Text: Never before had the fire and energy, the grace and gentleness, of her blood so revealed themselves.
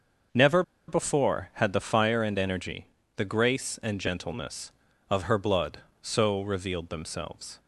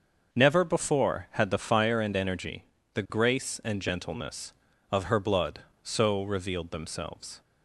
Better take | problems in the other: second | starts louder than the rest; until 1.6 s; 6 dB; noticeable in the second // pauses between "Never" and "before"; slight; at 0.6 s; 0.26 s long

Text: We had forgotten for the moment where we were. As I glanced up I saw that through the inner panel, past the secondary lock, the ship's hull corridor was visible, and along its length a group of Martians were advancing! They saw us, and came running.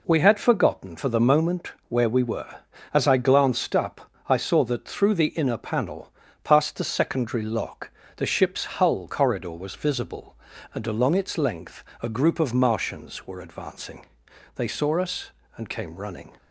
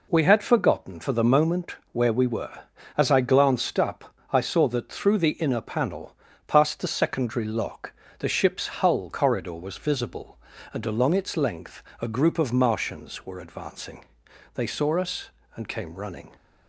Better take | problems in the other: neither | pauses between "moment" and "where"; slight; the same in both // pauses between "up" and "I"; slight; the same in both // pauses between "length" and "a"; slight; the same in both

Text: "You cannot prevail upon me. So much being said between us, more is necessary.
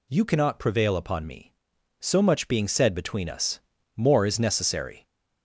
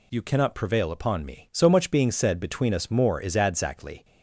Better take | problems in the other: first | says "adzactly" for "necessary"; at 3.3 s

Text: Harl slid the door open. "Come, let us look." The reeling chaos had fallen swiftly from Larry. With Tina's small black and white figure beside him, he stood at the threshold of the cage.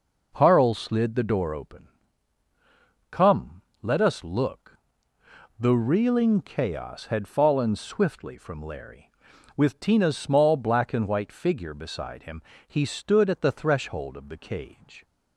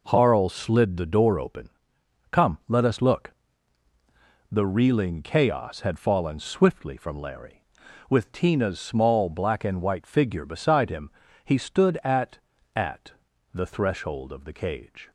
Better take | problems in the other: first | says "at" twice; at 12.7 s

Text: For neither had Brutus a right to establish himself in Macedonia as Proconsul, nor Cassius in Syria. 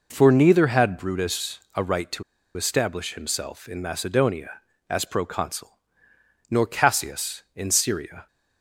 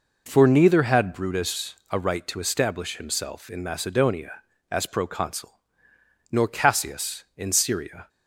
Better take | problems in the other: second | pauses between "to" and "establish"; slight; at 2.2 s; 0.33 s long

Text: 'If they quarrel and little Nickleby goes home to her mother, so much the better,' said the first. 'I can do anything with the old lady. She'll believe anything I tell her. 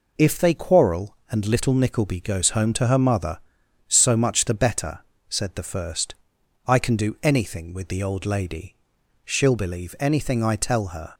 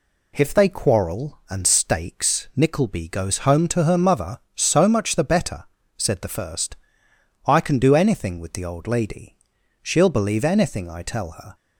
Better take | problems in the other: first | says "stakes" for "little"; at 1.6 s

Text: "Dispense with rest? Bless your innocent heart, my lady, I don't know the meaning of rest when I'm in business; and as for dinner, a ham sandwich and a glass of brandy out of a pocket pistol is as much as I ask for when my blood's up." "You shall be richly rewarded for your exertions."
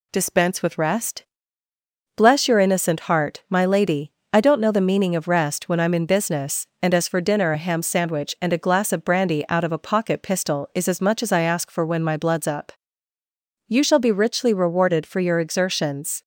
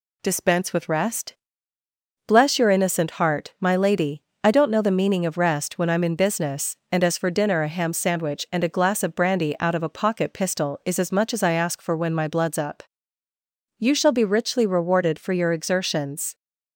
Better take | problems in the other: neither | none

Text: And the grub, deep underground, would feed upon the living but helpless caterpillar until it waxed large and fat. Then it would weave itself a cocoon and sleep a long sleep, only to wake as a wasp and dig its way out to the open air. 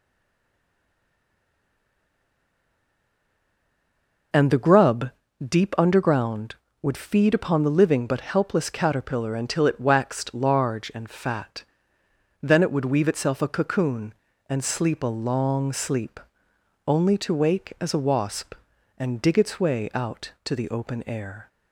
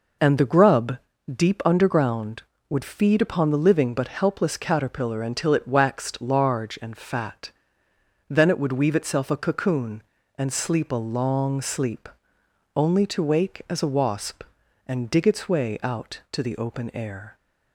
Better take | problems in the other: second | stays silent before the first word; strong; until 4.3 s; 4.3 s long

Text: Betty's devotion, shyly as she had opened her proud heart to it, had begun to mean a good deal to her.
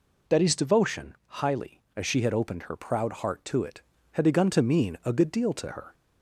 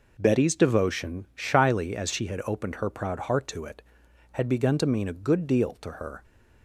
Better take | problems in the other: second | says "highly" for "shyly"; at 1.2 s

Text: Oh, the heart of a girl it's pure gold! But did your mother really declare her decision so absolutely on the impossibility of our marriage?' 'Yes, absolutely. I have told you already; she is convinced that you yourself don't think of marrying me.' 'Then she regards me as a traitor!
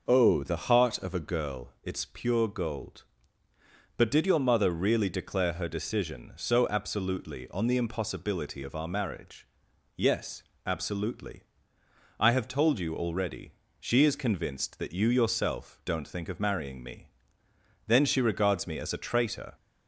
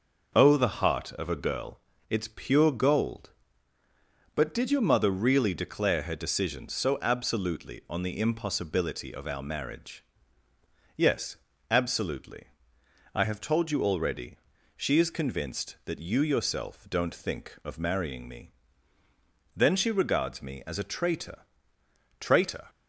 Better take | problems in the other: first | pauses between "girl" and "it's"; slight; at 1.7 s; 0.30 s long // says "traitor" twice; at 22.2 s

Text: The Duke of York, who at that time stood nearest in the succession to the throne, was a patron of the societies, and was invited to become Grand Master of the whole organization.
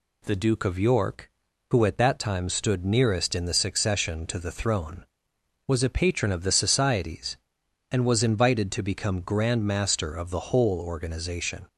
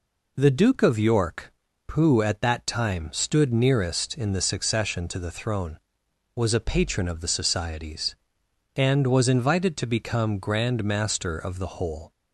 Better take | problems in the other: first | stops before "organization"; at 12.1 s

